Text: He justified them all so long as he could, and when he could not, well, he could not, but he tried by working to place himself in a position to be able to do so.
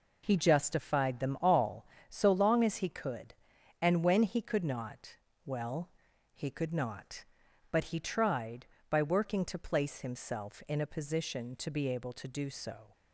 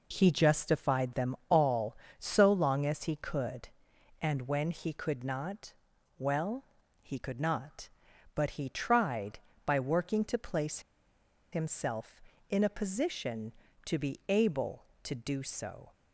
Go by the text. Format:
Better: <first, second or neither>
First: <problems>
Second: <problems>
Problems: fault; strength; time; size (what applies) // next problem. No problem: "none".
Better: first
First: none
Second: pauses between "place" and "himself"; noticeable; at 10.7 s; 0.72 s long